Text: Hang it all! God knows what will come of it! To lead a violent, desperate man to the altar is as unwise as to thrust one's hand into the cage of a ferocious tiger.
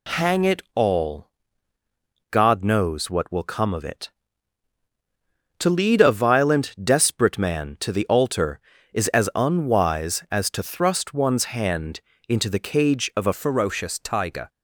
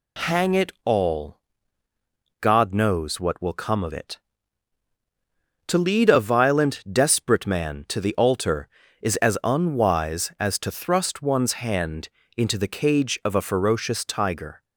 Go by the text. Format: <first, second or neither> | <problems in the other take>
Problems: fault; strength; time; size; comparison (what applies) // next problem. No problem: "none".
second | pauses between "hand" and "into"; slight; at 11.9 s; 0.28 s long; slight in the second // changes voice at "ferocious"; from 13.3 s on; 1.1 s long